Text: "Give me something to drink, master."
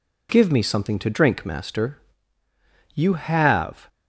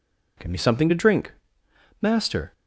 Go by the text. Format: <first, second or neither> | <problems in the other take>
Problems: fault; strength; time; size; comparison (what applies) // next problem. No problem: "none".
second | goes on to say "You have"; noticeable; from 2.9 s on; 0.96 s long